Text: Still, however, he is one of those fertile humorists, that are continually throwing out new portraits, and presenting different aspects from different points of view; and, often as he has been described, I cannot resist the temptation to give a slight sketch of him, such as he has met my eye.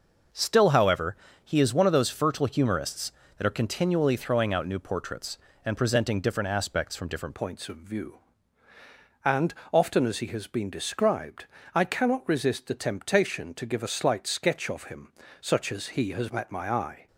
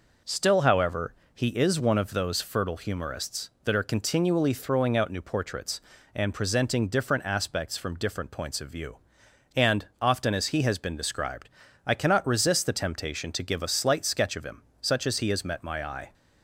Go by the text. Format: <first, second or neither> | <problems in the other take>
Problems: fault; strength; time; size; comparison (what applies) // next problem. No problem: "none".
second | changes voice at "points"; from 7.3 s on; 9.7 s long